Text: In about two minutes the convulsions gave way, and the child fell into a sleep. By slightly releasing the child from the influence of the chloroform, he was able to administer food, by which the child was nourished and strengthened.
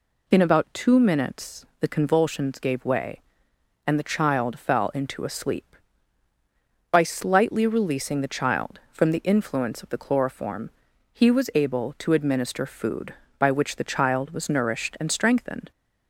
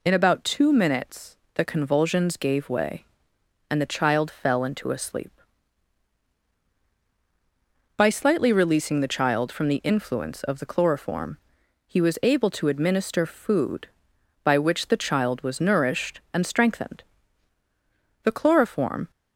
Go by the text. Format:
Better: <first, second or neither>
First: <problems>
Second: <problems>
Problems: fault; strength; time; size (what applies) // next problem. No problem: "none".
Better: first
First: none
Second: pauses between "minutes" and "the"; slight; at 1.3 s; 0.18 s long // goes on to say "The chloroform"; noticeable; from 18.2 s on; 0.88 s long